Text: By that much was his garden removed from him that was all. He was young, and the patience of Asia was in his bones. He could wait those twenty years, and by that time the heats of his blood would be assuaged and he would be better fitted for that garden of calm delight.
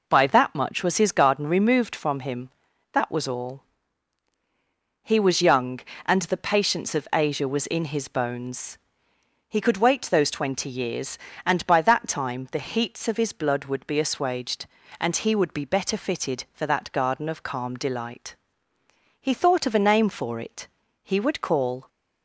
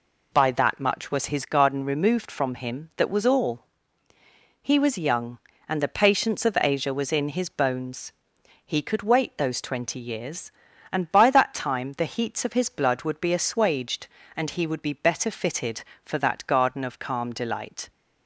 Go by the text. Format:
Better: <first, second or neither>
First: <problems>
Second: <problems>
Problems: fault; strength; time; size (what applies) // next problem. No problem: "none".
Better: second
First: goes on to say "He thought of a name for it he would call"; strong; from 19.1 s on; 2.6 s long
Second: none